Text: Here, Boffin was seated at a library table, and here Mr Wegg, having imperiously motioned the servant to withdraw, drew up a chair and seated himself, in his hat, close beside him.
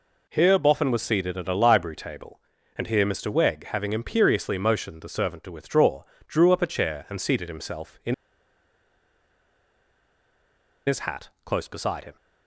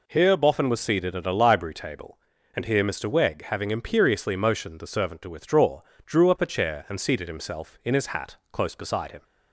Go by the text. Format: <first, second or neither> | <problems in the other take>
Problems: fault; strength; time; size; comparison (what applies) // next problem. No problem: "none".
second | pauses between "in" and "his"; strong; at 8.1 s; 2.7 s long